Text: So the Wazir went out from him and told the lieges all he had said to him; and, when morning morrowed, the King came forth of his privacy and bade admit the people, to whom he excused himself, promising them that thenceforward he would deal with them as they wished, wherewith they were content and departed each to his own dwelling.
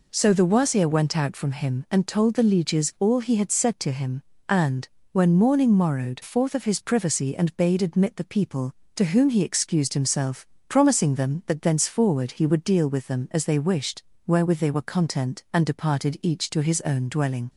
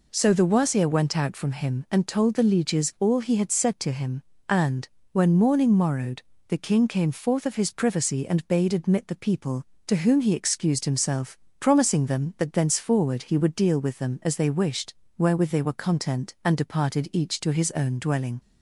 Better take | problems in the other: second | skips "the King came"; at 6.2 s

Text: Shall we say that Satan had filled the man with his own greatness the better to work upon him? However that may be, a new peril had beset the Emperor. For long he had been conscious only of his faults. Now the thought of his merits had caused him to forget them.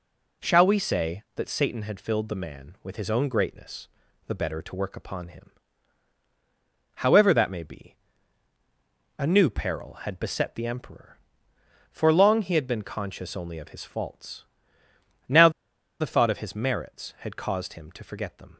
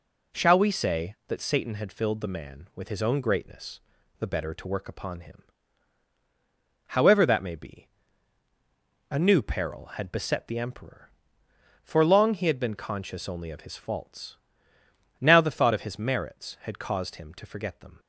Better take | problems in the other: second | pauses between "greatness" and "the"; at 3.8 s; 0.40 s long; also in the second // pauses between "Now" and "the"; noticeable; at 15.4 s; 0.50 s long

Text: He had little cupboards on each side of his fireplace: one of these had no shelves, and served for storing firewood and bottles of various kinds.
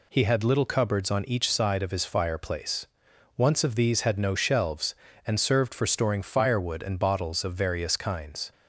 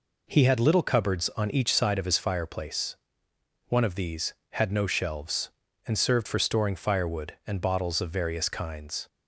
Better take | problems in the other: second | says "once" for "one"; at 3.3 s

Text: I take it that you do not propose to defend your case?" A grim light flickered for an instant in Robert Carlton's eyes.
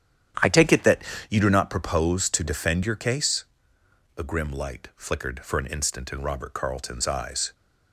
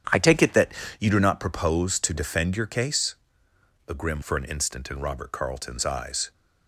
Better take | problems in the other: first | starts louder than the rest; strong; until 1.3 s; 9.5 dB; strong in the first // pauses between "that" and "you"; slight; at 0.7 s; 0.28 s long; slight in the first // skips "light flickered"; at 4.2 s

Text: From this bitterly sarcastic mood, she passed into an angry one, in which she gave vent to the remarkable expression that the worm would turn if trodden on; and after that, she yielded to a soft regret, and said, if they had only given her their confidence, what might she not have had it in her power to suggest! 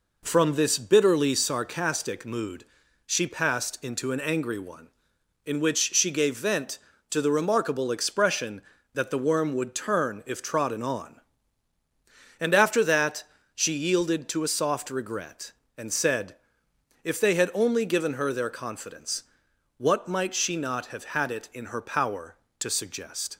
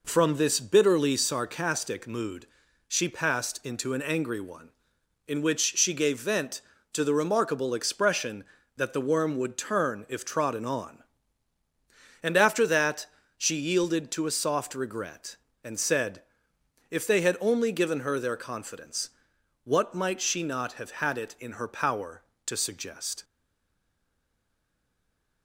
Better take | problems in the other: first | stays silent after the last word; from 23.2 s on; 2.2 s long

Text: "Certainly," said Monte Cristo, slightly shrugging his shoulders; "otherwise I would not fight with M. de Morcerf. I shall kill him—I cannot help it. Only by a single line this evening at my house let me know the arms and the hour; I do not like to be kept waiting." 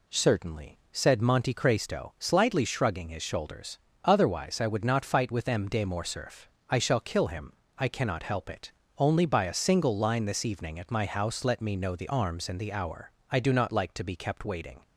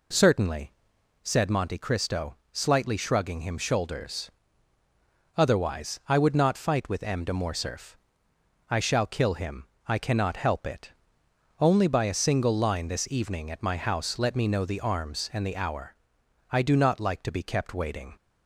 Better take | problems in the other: first | says "him" for "his"; at 3.3 s

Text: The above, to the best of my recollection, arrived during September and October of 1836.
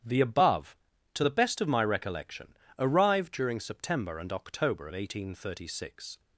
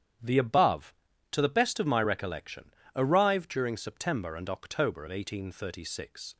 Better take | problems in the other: neither | starts louder than the rest; strong; the same in both

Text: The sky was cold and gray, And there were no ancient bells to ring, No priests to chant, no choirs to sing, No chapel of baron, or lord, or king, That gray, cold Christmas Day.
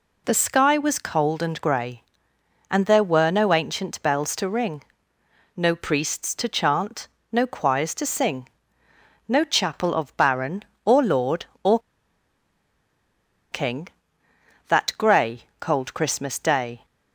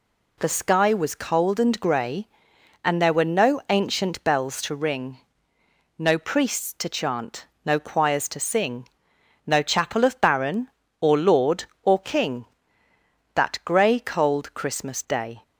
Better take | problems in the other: second | pauses between "or" and "king"; strong; at 11.7 s; 1.7 s long

